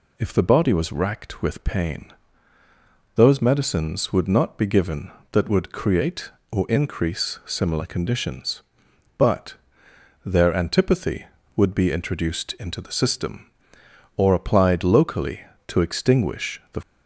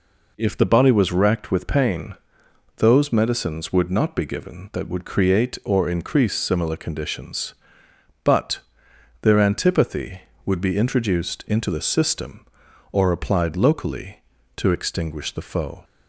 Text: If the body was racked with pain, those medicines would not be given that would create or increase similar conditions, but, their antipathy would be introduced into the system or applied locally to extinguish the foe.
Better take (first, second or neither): second